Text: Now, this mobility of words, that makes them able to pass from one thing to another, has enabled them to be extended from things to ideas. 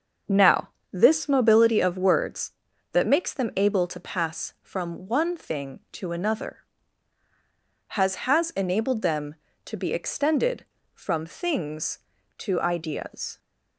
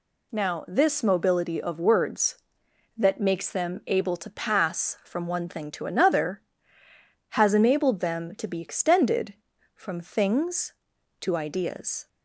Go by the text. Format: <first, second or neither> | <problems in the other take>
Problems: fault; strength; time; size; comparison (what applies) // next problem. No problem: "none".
second | starts louder than the rest; until 1.5 s; 6.5 dB // says "has" twice; at 8.2 s